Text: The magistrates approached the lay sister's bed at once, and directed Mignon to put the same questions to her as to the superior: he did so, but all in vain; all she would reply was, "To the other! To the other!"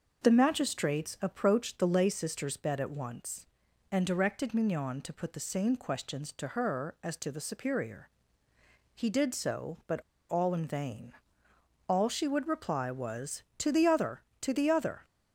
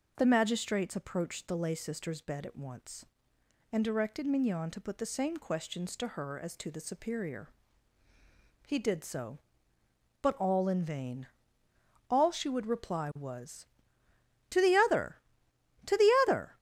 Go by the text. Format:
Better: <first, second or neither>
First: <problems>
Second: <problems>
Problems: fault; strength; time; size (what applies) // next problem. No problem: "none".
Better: second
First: starts louder than the rest; noticeable; until 1.2 s; 6 dB // pauses between "but" and "all"; slight; at 9.9 s; 0.30 s long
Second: none